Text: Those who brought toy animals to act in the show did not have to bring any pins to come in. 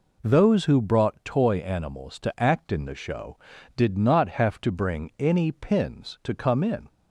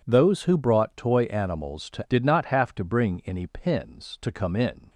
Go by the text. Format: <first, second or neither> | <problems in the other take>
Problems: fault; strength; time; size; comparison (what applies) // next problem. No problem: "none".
first | skips "act in the show"; at 2.0 s